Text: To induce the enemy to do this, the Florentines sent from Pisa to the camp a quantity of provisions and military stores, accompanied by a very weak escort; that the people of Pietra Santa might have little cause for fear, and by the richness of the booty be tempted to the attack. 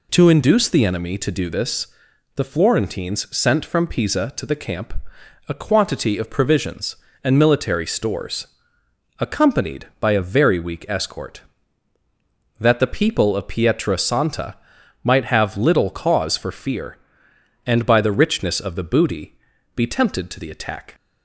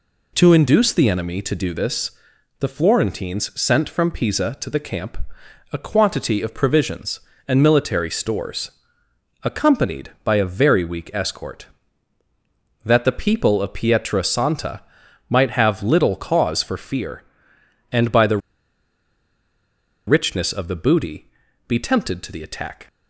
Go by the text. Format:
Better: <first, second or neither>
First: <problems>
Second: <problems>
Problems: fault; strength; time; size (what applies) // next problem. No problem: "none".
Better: first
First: pauses between "camp" and "a"; noticeable; at 4.9 s; 0.56 s long // pauses between "Santa" and "might"; noticeable; at 14.5 s; 0.46 s long // pauses between "booty" and "be"; at 19.3 s; 0.40 s long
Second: pauses between "camp" and "a"; noticeable; at 5.1 s; 0.56 s long // pauses between "Santa" and "might"; noticeable; at 14.8 s; 0.46 s long // pauses between "the" and "richness"; strong; at 18.3 s; 1.6 s long // pauses between "booty" and "be"; at 21.2 s; 0.40 s long